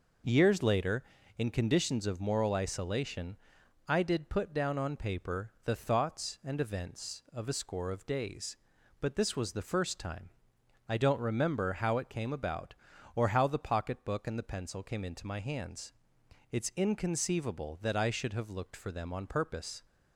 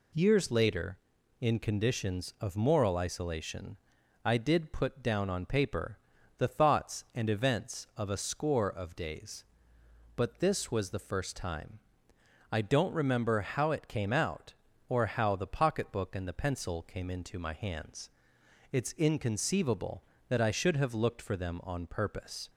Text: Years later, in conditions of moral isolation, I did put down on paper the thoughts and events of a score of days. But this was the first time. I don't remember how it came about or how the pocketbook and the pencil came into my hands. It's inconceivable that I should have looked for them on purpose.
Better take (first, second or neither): first